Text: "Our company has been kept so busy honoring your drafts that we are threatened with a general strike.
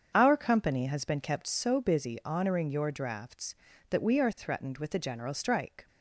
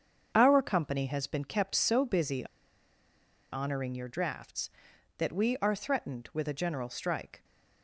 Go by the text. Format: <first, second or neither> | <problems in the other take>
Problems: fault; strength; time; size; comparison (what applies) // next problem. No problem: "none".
first | starts louder than the rest; until 1.3 s; 7 dB; strong in the first // pauses between "busy" and "honoring"; at 2.4 s; 1.0 s long